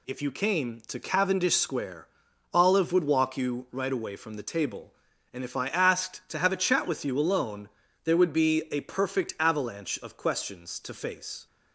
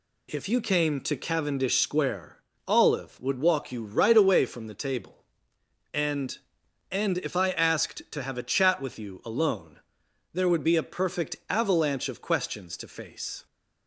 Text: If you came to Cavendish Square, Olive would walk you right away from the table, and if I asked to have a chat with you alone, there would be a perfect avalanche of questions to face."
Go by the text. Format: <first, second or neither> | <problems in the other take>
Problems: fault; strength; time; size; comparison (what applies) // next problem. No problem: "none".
first | says "and" twice; at 6.9 s